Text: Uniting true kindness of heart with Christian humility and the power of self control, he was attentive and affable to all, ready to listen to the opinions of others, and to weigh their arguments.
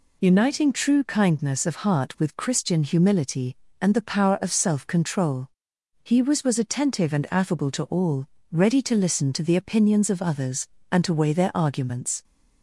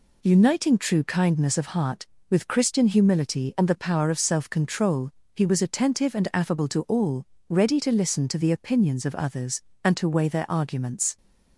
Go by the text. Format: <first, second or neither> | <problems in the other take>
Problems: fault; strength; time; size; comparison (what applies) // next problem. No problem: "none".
second | says "was" twice; at 6.4 s